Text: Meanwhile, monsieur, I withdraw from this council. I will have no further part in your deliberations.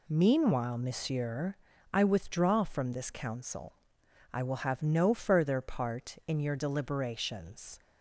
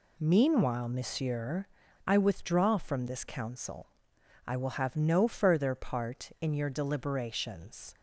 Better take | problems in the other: neither | none

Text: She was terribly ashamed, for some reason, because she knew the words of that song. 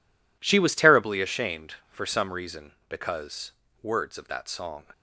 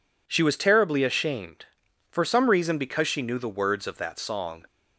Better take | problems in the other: second | skips "she knew the"; at 3.6 s

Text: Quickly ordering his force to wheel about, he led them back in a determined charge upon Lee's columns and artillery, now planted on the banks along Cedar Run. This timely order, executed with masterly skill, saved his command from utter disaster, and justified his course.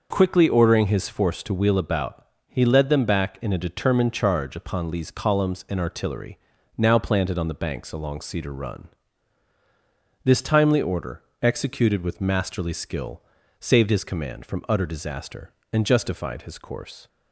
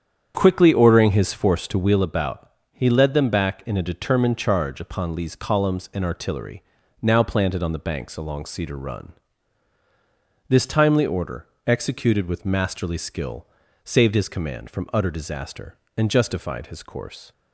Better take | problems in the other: first | starts louder than the rest; strong; until 2.0 s; 8.5 dB

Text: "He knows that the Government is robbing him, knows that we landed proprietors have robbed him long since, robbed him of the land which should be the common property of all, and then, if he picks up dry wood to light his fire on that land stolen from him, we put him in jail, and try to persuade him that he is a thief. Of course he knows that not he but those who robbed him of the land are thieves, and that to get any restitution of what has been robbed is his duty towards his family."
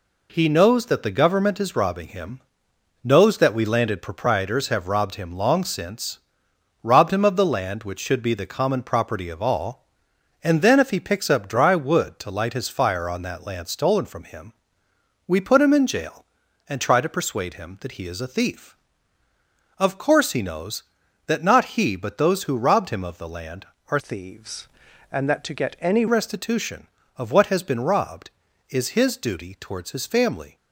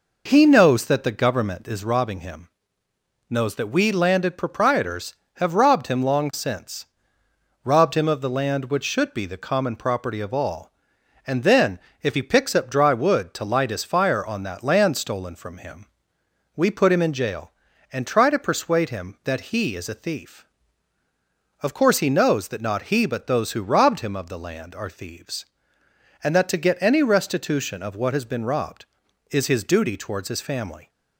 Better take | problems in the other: second | changes voice from "thieves" to "any"; from 23.9 to 26.0 s; 2.1 s long

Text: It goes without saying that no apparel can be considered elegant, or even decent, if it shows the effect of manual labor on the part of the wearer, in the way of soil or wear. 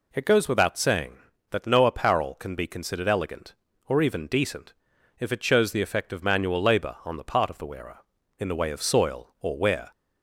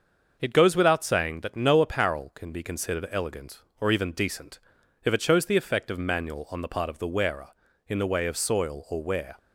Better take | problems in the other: first | starts louder than the rest; until 1.4 s; 6.5 dB // skips "labor"; at 6.4 s

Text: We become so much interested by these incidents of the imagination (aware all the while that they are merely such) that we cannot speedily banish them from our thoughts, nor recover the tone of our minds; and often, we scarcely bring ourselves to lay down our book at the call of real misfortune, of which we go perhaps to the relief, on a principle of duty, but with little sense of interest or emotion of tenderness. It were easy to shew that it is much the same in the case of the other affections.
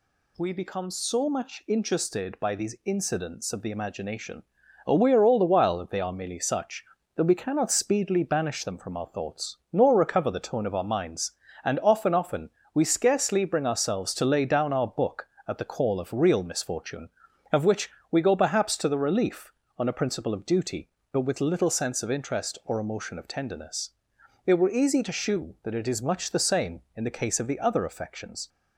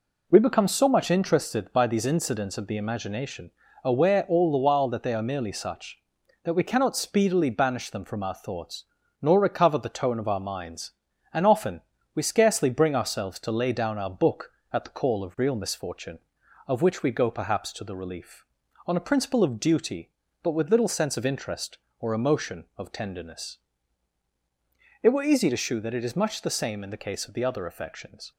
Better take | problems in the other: second | says "often" twice; at 12.1 s // pauses between "which" and "we"; slight; at 17.9 s; 0.20 s long

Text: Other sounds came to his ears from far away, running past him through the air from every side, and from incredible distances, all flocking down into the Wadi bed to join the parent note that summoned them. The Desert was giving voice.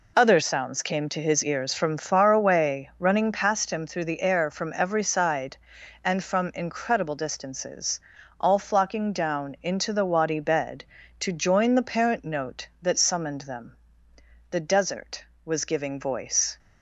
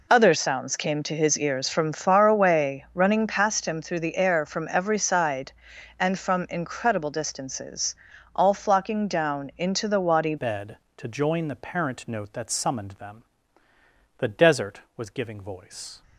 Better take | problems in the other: first | changes voice at "bed"; from 10.3 s on; 5.7 s long

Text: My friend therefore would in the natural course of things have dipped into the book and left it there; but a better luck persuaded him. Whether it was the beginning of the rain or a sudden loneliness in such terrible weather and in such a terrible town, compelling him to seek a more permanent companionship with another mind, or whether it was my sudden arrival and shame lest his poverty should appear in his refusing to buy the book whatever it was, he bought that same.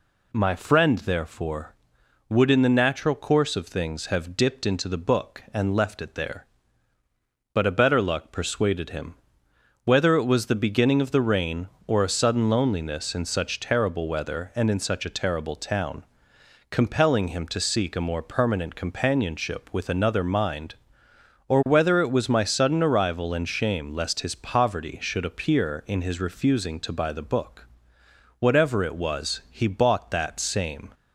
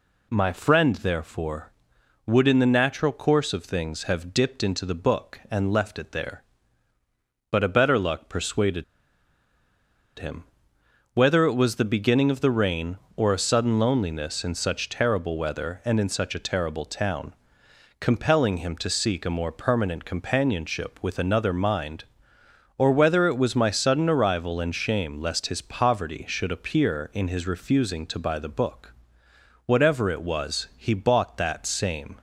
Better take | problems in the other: first | pauses between "persuaded" and "him"; strong; at 8.8 s; 1.3 s long // pauses between "book" and "whatever"; noticeable; at 28.8 s; 0.76 s long; noticeable in the first

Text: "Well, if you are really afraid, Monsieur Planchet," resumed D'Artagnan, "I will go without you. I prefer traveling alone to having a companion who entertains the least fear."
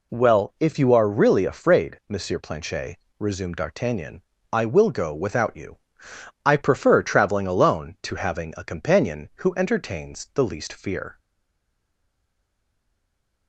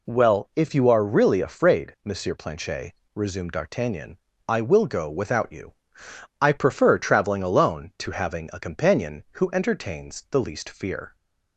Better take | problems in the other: second | stays silent after the last word; from 11.1 s on; 2.3 s long

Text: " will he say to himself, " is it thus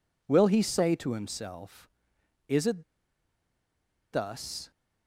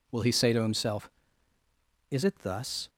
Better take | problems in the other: second | pauses between "it" and "thus"; strong; at 2.8 s; 1.2 s long

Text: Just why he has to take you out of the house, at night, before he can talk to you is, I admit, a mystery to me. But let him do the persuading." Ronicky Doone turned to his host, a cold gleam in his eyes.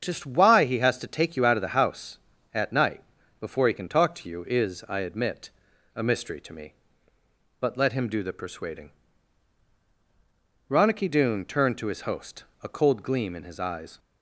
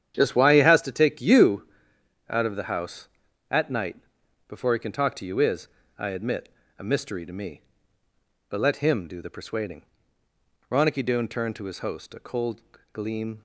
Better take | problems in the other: first | starts louder than the rest; strong; until 1.2 s; 9.5 dB; strong in the first // pauses between "you" and "out"; noticeable; at 1.6 s; 0.64 s long // pauses between "cold" and "gleam"; slight; at 12.6 s; 0.30 s long // stops before "in his eyes"; at 13.3 s

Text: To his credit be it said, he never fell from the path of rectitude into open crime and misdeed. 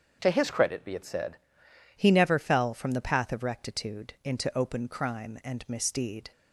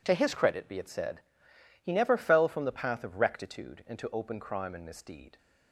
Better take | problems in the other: second | starts louder than the rest; until 1.2 s; 7 dB // changes voice at "he"; from 1.9 s on; 4.4 s long

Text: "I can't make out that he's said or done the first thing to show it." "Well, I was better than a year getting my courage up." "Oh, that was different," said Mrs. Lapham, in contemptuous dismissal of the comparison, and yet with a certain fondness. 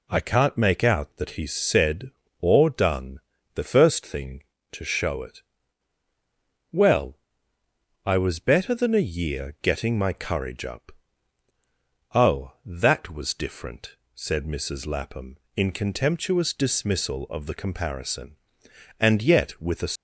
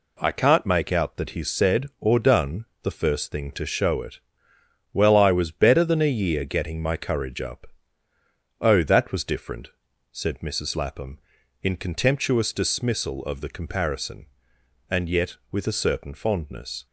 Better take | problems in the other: second | pauses between "done" and "the"; slight; at 3.1 s; 0.36 s long; slight in the second // stops before "certain fondness"; at 19.9 s

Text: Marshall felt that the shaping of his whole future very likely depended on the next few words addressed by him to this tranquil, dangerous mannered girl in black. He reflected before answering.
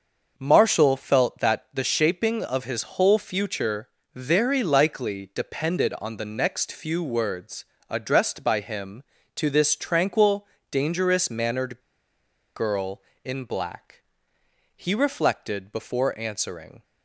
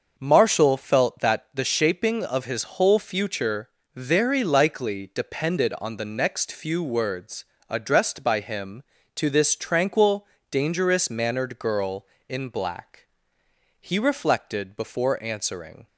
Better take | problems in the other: second | starts louder than the rest; until 1.3 s; 6 dB; also in the second // pauses between "future" and "very"; slight; at 3.8 s; 0.26 s long; slight in the second // pauses between "words" and "addressed"; slight; at 7.6 s; 0.24 s long; slight in the second // pauses between "mannered" and "girl"; noticeable; at 11.7 s; 0.75 s long

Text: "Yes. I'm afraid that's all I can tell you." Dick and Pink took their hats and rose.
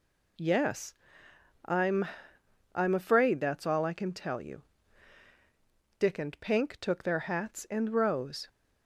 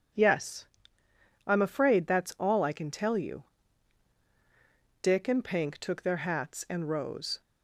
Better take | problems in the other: second | says "I'm" twice; at 2.7 s

